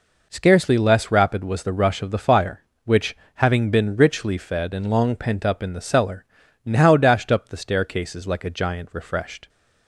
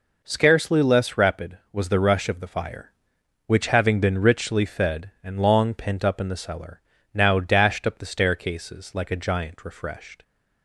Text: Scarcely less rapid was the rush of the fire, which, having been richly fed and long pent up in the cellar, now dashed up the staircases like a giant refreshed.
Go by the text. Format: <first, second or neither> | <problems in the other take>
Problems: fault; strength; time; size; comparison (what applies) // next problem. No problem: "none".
neither | none